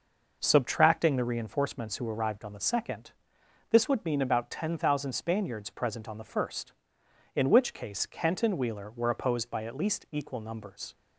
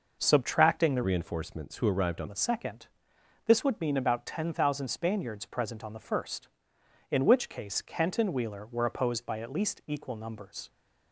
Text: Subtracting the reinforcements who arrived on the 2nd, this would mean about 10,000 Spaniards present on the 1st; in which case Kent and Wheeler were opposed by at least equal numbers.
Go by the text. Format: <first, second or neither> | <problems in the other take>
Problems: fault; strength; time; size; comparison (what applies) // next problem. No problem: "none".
first | changes voice from "reinforcements" to "on"; from 1.0 to 2.2 s; 1.2 s long